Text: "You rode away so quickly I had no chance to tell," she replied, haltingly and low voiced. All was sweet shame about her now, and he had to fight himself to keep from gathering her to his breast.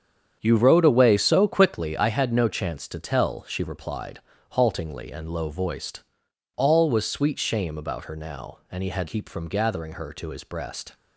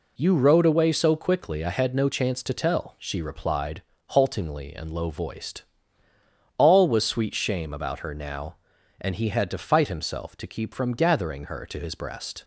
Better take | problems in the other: second | starts louder than the rest; strong; until 1.4 s; 8 dB // skips "to fight himself to"; at 9.0 s

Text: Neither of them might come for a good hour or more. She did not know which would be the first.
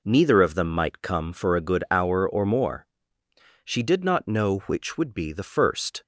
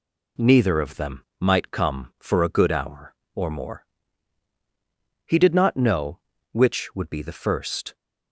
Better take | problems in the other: first | pauses between "them" and "might"; slight; at 1.2 s; 0.16 s long // says "He" for "She"; at 5.2 s

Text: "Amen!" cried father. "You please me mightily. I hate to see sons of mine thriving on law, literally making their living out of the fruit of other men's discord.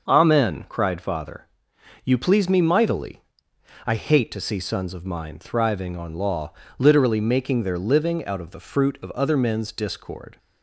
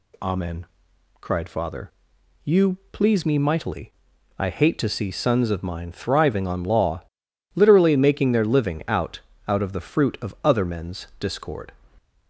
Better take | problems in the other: first | pauses between "You" and "please"; slight; at 2.7 s; 0.16 s long // says "out" twice; at 9.4 s

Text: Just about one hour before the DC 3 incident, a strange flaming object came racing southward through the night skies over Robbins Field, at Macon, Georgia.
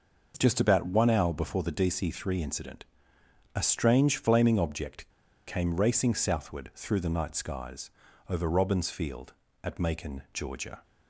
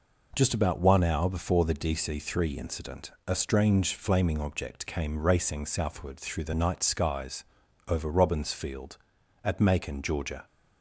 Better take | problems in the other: second | pauses between "object" and "came"; at 5.0 s; 0.39 s long // pauses between "skies" and "over"; at 7.9 s; 0.40 s long; also in the second

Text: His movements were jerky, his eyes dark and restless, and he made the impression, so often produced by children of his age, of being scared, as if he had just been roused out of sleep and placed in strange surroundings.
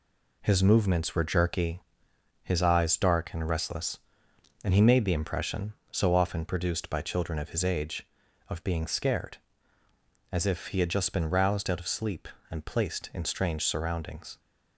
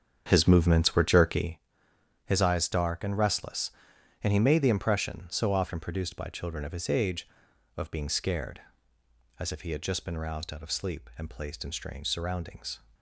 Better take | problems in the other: first | starts louder than the rest; strong; until 1.5 s; 7.5 dB

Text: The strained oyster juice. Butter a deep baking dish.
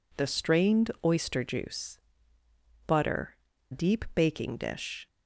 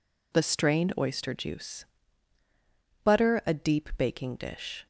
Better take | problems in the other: second | skips "a"; at 3.5 s

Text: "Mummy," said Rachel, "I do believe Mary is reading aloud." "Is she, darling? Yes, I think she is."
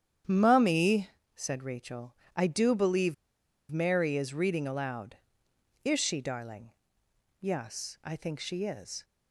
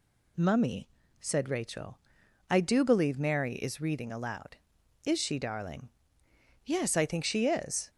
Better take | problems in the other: second | starts louder than the rest; strong; until 1.5 s; 9 dB // pauses between "believe" and "Mary"; noticeable; at 3.1 s; 0.55 s long

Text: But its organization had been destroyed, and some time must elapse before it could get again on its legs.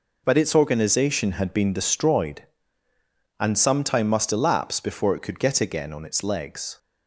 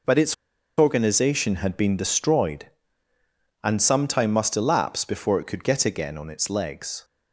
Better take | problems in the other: first | pauses between "its" and "organization"; at 0.3 s; 0.43 s long

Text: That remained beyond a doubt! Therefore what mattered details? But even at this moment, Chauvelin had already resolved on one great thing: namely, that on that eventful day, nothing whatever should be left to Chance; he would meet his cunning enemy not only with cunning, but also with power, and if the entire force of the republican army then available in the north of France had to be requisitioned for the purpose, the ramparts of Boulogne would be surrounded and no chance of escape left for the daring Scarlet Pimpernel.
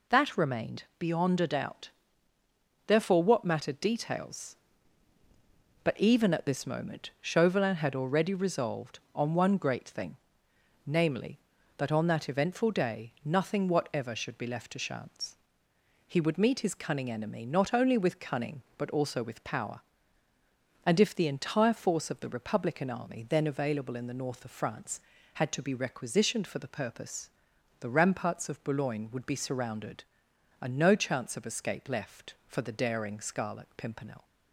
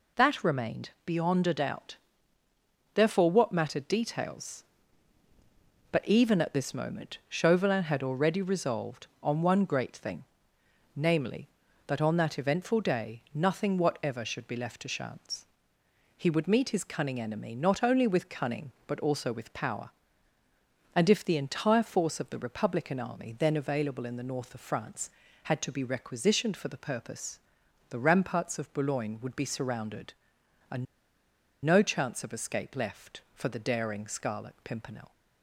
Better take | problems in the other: first | pauses between "remained" and "beyond"; slight; at 0.8 s; 0.16 s long; slight in the first // pauses between "and" and "no"; noticeable; at 30.8 s; 0.79 s long

